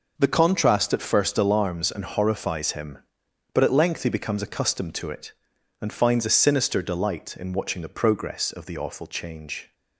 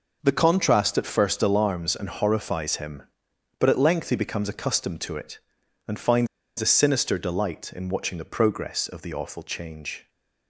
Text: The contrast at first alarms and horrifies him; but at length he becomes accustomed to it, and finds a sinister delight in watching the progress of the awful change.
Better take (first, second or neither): first